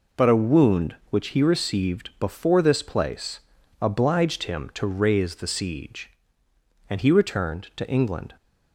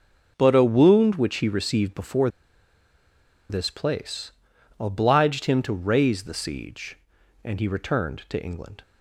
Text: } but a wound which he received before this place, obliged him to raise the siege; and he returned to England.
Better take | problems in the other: first | pauses between "before" and "this"; at 2.2 s; 1.2 s long

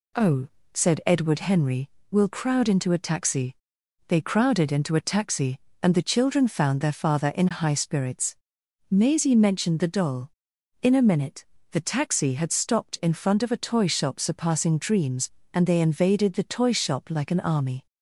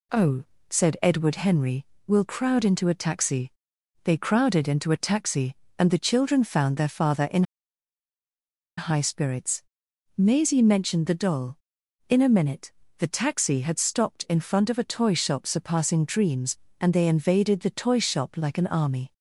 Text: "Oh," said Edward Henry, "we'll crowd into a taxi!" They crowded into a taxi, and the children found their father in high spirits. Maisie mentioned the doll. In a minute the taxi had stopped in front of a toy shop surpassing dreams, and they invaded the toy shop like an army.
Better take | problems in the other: first | pauses between "in" and "high"; strong; at 7.4 s; 1.3 s long // pauses between "minute" and "the"; slight; at 12.7 s; 0.24 s long; slight in the first

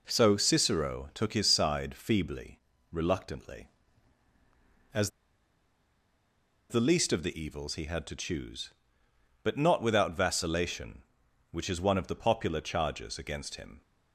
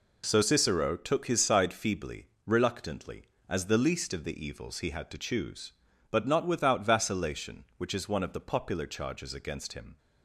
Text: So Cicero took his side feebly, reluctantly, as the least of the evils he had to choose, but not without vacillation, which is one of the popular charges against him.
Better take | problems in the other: second | pauses between "as" and "the"; strong; at 5.0 s; 1.5 s long

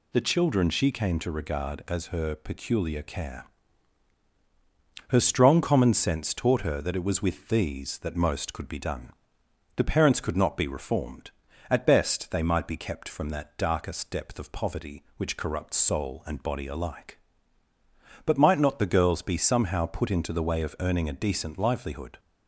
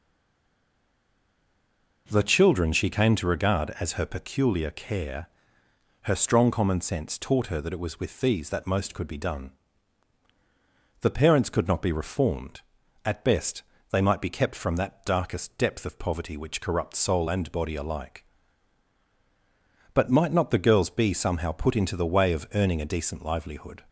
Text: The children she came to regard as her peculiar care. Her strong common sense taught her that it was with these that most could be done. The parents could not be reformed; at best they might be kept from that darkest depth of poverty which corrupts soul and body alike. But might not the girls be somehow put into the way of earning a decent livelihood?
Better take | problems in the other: first | stays silent before the first word; noticeable; until 2.0 s; 2.0 s long // pauses between "best" and "they"; slight; at 13.6 s; 0.28 s long

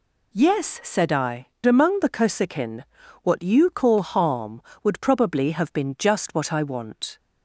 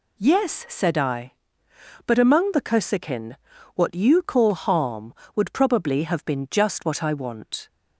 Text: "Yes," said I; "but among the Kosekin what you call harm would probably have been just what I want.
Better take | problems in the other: second | skips "but"; at 1.5 s // pauses between "Kosekin" and "what"; at 2.8 s; 0.40 s long; also in the second

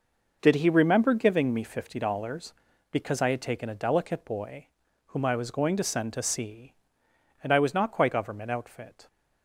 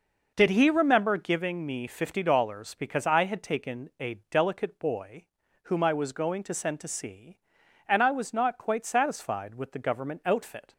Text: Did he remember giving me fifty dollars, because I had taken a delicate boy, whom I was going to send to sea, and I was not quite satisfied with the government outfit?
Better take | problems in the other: second | skips "satisfied with the"; at 8.1 s

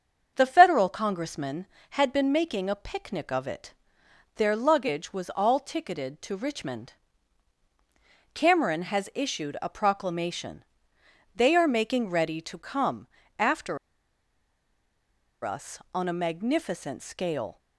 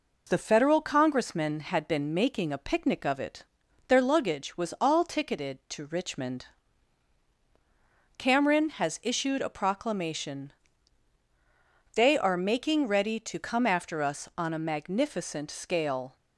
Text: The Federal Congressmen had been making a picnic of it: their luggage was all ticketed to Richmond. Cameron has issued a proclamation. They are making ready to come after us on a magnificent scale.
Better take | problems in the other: second | starts louder than the rest; strong; until 1.3 s; 7 dB // pauses between "come" and "after"; slight; at 13.0 s; 0.32 s long // pauses between "after" and "us"; strong; at 13.7 s; 1.6 s long

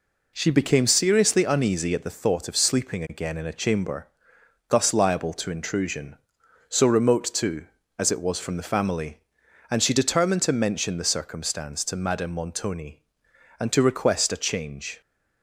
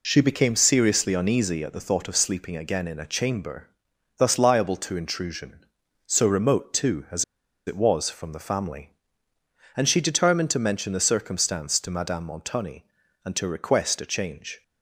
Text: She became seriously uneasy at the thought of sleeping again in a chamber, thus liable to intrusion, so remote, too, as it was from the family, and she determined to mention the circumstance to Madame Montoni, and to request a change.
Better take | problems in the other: first | pauses between "as" and "it"; at 7.2 s; 0.42 s long

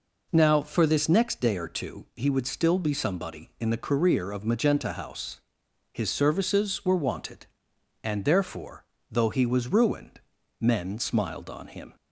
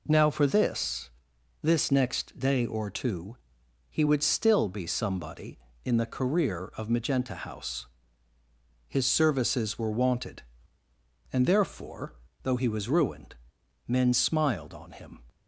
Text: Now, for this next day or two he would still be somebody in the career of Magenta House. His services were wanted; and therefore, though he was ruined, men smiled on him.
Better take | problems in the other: first | says "this" twice; at 1.6 s // pauses between "two" and "he"; noticeable; at 3.3 s; 0.52 s long

